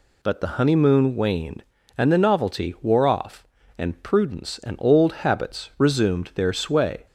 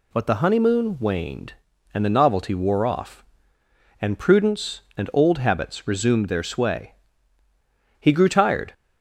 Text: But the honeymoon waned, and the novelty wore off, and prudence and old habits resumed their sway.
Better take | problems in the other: first | goes on to say "He grew tired"; noticeable; from 7.9 s on; 0.74 s long

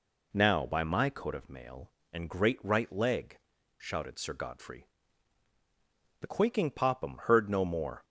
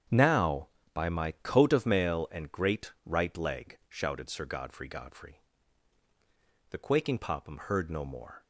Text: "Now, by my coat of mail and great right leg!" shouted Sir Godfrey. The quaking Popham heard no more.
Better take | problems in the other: first | starts louder than the rest; strong; until 1.4 s; 8 dB // says "Godfrey" twice; at 4.8 s

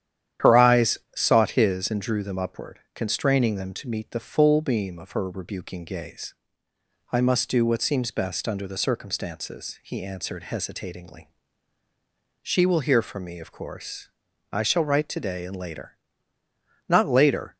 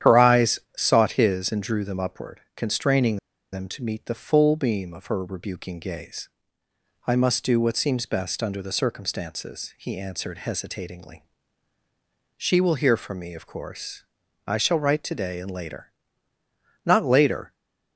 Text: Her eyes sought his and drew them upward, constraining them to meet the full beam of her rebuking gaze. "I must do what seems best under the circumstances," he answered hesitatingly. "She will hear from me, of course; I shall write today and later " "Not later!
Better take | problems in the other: first | starts louder than the rest; strong; until 1.2 s; 10 dB; strong in the first // pauses between "eyes" and "sought"; slight; at 0.5 s; 0.18 s long; slight in the first // pauses between "constraining" and "them"; slight; at 3.1 s; 0.34 s long

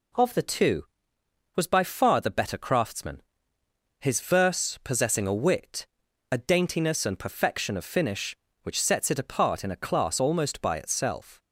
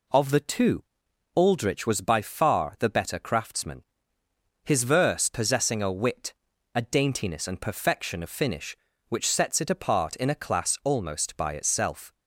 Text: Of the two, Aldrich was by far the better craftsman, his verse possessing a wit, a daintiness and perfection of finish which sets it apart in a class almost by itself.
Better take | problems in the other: second | skips "Aldrich"; at 1.1 s

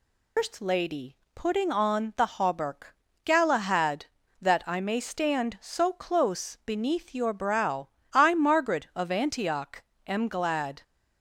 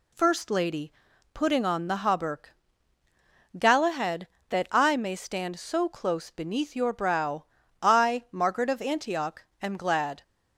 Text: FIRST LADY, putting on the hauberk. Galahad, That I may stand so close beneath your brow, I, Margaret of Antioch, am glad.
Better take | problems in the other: second | loses the start of "FIRST"; at 0.3 s; 170 ms

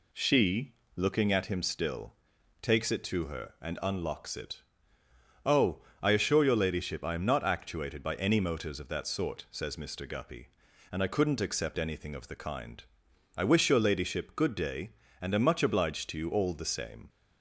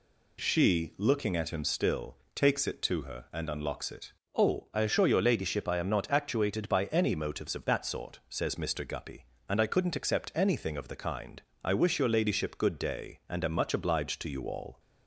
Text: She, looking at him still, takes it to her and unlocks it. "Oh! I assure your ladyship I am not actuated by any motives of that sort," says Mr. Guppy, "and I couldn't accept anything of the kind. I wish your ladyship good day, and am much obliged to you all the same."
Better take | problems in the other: first | stops before "the same"; at 14.7 s

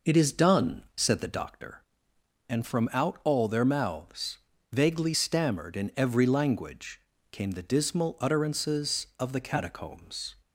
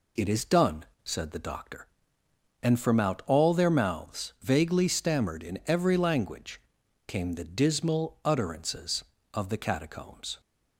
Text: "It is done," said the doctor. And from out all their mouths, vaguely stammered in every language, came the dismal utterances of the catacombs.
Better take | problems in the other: second | starts louder than the rest; noticeable; until 1.5 s; 5 dB

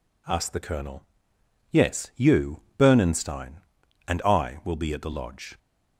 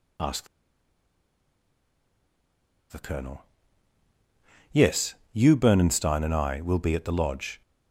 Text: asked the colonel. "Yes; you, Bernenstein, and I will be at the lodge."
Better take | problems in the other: first | pauses between "asked" and "the"; strong; at 0.4 s; 2.4 s long

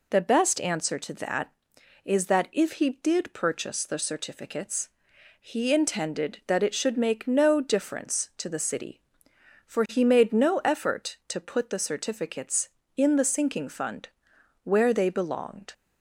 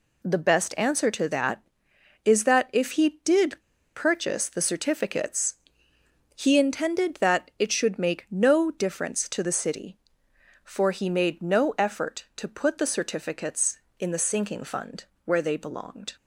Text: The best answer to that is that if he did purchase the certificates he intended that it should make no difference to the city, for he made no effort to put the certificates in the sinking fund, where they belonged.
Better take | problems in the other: first | pauses between "did" and "purchase"; slight; at 3.5 s; 0.35 s long // pauses between "certificates" and "he"; noticeable; at 5.5 s; 0.82 s long; noticeable in the first

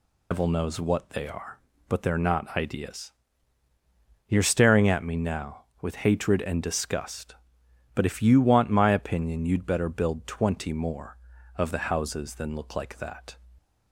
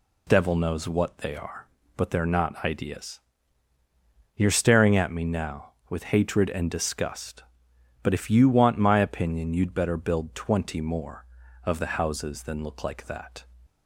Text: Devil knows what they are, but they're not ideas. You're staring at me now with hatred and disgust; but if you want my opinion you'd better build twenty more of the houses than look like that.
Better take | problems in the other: second | loses the start of "Devil"; at 0.3 s; 120 ms

